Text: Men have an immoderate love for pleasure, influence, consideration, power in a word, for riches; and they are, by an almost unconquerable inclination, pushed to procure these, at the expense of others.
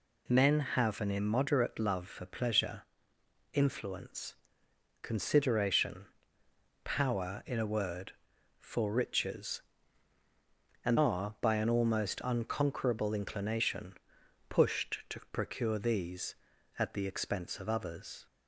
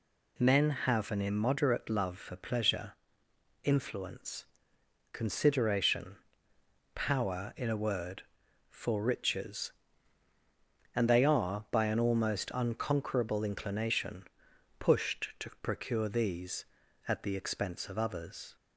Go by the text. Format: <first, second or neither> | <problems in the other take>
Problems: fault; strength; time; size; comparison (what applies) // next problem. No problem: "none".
second | skips "they"; at 10.9 s